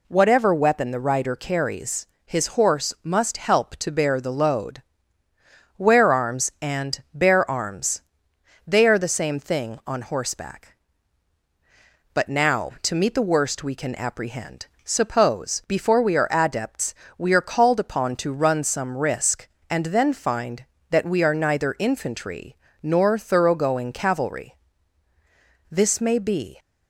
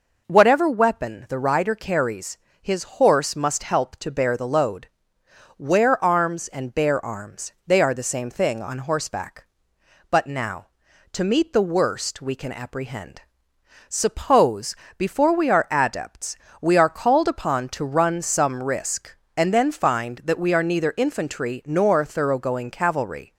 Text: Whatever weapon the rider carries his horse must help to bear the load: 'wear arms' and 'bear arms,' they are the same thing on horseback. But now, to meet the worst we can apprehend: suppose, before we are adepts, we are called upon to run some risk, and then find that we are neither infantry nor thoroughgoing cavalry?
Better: second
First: pauses between "carries" and "his"; slight; at 2.0 s; 0.20 s long // pauses between "infantry" and "nor"; slight; at 22.5 s; 0.26 s long // goes on to say "This may be"; noticeable; from 25.7 s on; 0.88 s long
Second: pauses between "carries" and "his"; slight; at 2.3 s; 0.24 s long

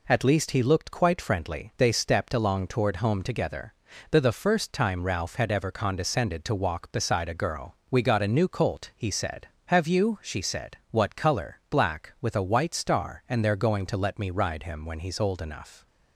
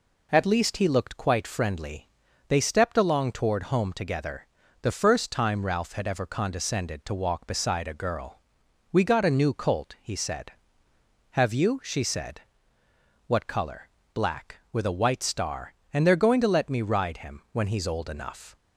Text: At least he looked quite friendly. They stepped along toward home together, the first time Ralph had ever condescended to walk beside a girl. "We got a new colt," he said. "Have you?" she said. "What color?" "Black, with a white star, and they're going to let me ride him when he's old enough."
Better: second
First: says "the" twice; at 4.2 s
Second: none

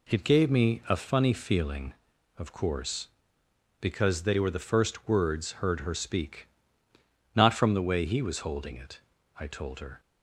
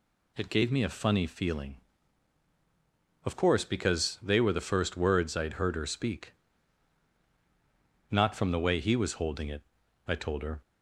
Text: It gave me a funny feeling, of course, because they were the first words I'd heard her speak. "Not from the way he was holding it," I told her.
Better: second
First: skips "I'd"; at 5.5 s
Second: none

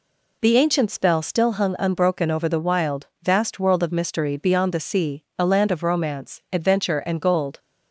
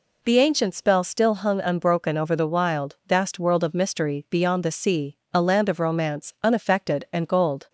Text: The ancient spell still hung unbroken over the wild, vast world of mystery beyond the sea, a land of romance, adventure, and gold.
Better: first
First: none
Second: says "unaffected" for "adventure"; at 6.4 s

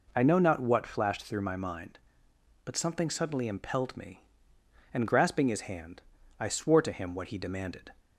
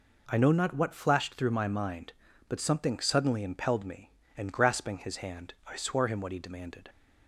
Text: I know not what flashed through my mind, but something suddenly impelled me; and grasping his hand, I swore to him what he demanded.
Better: first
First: none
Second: skips "to"; at 6.0 s

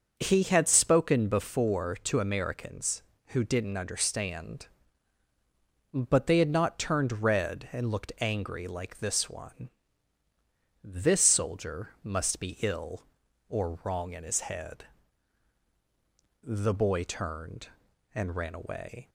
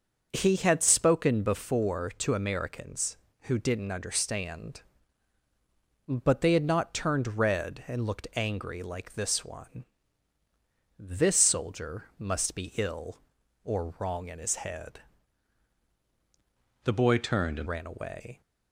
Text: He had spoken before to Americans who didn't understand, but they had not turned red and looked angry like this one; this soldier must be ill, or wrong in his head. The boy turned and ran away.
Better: first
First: starts louder than the rest; until 1.2 s; 6 dB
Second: starts louder than the rest; until 1.3 s; 6.5 dB // changes voice from "The" to "and"; from 16.8 to 17.6 s; 0.8 s long

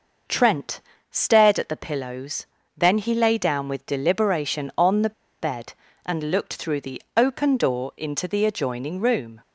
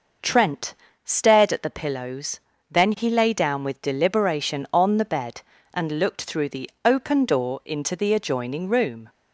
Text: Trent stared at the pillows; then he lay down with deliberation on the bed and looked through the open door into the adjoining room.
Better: second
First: pauses between "Trent" and "stared"; slight; at 0.8 s; 0.32 s long // pauses between "the" and "bed"; slight; at 5.1 s; 0.29 s long // pauses between "the" and "open"; slight; at 7.0 s; 0.16 s long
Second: pauses between "Trent" and "stared"; slight; at 0.7 s; 0.32 s long // pauses between "the" and "open"; slight; at 6.6 s; 0.16 s long

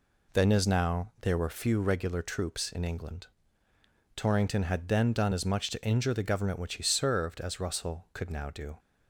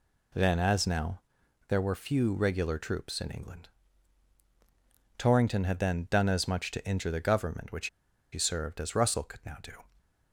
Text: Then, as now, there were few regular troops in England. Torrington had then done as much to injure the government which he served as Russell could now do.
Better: first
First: none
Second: pauses between "which" and "he"; at 7.8 s; 0.45 s long

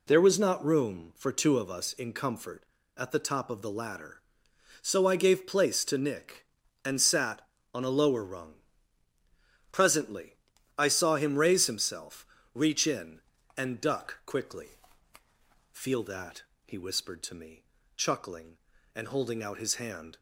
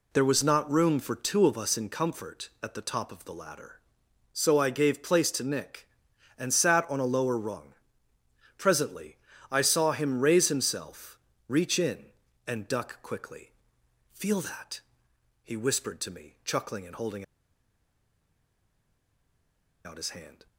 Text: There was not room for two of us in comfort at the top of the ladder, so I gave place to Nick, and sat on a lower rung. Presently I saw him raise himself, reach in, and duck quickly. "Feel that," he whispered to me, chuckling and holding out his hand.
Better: first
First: pauses between "Presently" and "I"; at 10.3 s; 0.40 s long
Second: pauses between "Presently" and "I"; slight; at 9.1 s; 0.34 s long // pauses between "holding" and "out"; strong; at 17.2 s; 2.6 s long

